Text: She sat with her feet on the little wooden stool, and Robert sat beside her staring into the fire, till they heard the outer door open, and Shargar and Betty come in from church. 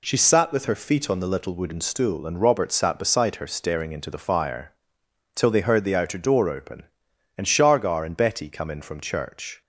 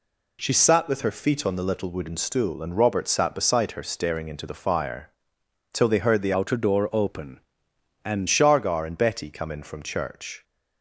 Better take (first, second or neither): first